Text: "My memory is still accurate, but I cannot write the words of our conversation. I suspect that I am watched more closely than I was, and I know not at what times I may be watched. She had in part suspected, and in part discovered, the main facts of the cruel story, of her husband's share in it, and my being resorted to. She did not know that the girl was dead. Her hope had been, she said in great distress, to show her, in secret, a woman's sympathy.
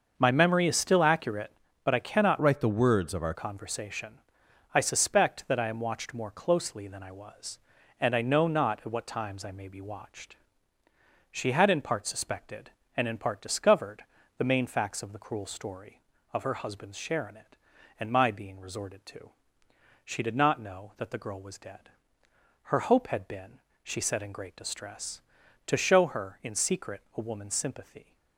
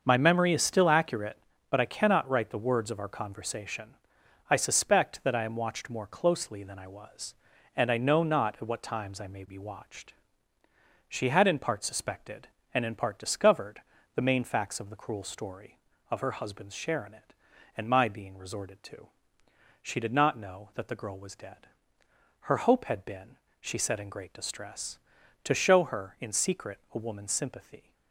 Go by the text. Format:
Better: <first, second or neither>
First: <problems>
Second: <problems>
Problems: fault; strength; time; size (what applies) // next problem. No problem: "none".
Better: second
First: starts louder than the rest; until 1.2 s; 6.5 dB // changes voice from "write" to "our"; from 2.4 to 3.3 s; 0.9 s long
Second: starts louder than the rest; until 1.0 s; 6.5 dB